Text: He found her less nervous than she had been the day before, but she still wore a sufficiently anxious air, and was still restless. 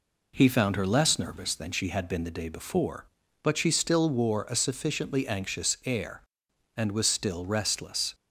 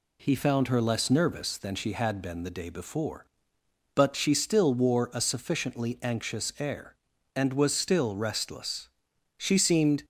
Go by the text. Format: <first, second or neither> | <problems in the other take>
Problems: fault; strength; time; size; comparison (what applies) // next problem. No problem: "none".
first | goes on to say "She seemed"; noticeable; from 9.3 s on; 0.64 s long